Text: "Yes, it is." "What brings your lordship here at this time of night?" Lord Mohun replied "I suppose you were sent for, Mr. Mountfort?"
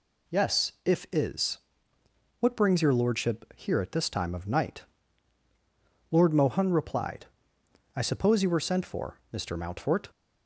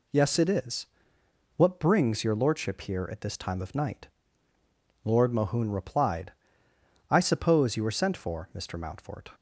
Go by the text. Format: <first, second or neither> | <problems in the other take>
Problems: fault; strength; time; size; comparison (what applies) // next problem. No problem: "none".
second | says "if" for "it"; at 0.8 s // pauses between "replied" and "I"; noticeable; at 7.2 s; 0.68 s long; noticeable in the second